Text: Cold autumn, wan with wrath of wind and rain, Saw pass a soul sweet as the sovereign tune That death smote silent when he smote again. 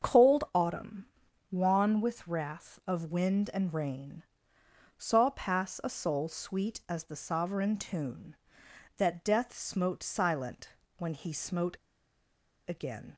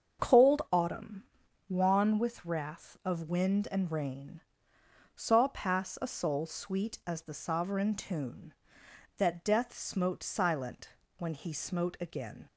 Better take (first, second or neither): second